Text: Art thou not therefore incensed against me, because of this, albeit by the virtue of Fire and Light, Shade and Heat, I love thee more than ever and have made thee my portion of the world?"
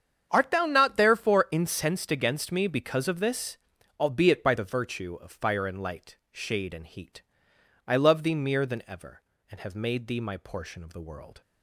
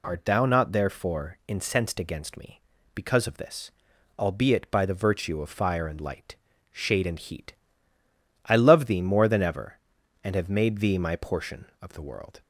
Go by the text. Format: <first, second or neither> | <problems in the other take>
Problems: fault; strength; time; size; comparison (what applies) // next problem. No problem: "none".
second | starts louder than the rest; strong; until 1.3 s; 8 dB // says "mere" for "more"; at 8.3 s